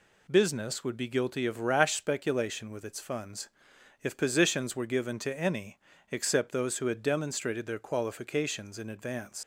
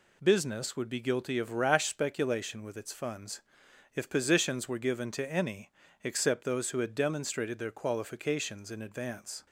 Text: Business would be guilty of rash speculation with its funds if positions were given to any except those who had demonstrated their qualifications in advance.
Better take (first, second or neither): second